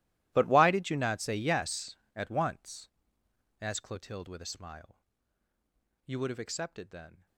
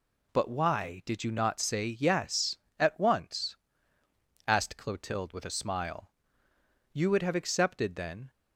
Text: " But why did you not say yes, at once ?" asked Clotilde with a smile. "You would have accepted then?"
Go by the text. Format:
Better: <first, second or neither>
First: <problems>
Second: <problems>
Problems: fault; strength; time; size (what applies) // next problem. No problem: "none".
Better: second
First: gets quieter; strong; throughout; 21 dB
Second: none